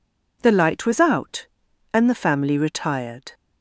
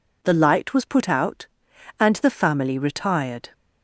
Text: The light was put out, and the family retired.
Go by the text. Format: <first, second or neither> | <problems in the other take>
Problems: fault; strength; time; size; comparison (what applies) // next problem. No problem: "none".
second | skips "put"; at 1.0 s